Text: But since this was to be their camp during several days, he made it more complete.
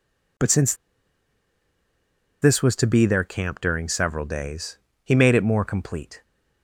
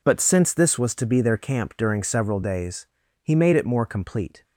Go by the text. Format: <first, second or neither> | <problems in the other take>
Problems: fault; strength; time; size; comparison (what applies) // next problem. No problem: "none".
second | pauses between "since" and "this"; strong; at 0.7 s; 1.6 s long